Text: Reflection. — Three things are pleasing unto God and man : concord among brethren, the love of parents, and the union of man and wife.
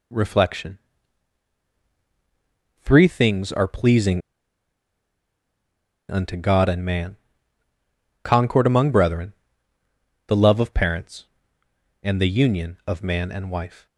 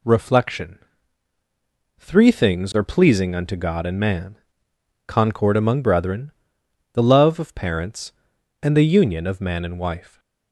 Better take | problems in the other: second | pauses between "pleasing" and "unto"; strong; at 4.2 s; 1.8 s long

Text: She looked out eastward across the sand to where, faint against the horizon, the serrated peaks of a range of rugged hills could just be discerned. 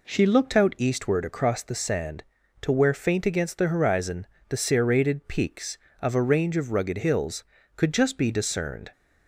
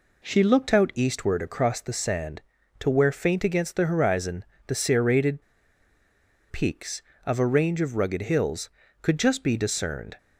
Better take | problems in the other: first | pauses between "serrated" and "peaks"; at 5.4 s; 1.0 s long

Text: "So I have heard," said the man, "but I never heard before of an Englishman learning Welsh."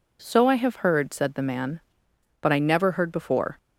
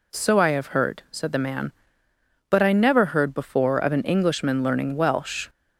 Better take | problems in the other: second | stops before "of an Englishman learning Welsh"; at 3.5 s

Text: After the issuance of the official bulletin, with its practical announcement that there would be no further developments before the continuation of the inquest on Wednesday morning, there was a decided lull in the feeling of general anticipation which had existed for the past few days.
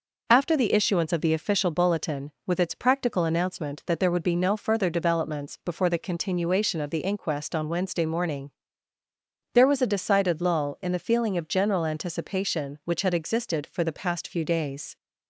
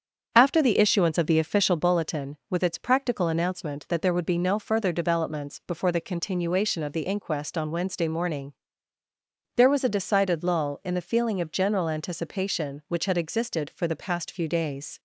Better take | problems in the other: first | starts louder than the rest; strong; until 1.9 s; 7.5 dB

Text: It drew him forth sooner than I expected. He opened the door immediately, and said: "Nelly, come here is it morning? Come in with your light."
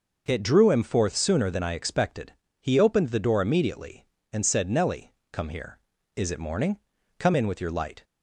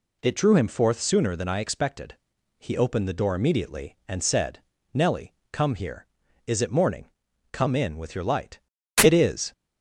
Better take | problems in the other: first | goes on to say "It is"; from 9.0 s on; 0.50 s long

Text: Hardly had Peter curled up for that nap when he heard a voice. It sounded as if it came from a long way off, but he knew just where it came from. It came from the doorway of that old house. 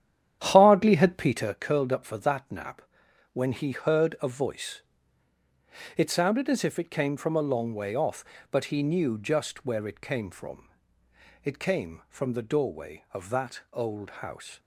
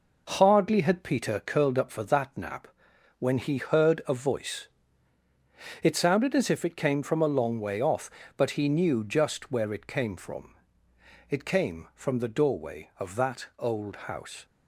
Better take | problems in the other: second | starts louder than the rest; strong; until 1.5 s; 10 dB // pauses between "nap" and "when"; noticeable; at 2.8 s; 0.50 s long; noticeable in the second

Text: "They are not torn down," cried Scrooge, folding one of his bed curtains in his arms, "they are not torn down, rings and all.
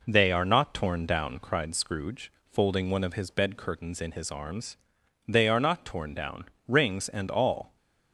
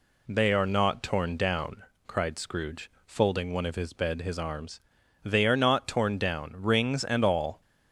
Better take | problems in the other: first | skips "curtains in"; at 4.2 s

